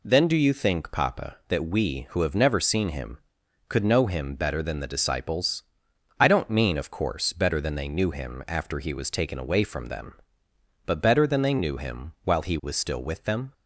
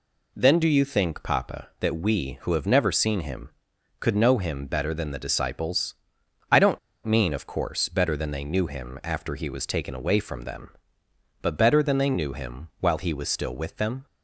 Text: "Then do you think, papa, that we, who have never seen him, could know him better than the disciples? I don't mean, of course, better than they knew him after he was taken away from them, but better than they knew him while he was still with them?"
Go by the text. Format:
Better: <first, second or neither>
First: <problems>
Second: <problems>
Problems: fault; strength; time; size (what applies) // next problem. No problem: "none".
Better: first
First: none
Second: pauses between "don't" and "mean"; slight; at 6.7 s; 0.26 s long